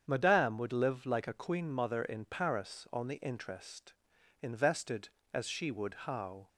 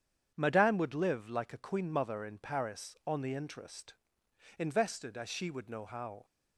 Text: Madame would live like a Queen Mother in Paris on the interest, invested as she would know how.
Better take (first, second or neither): second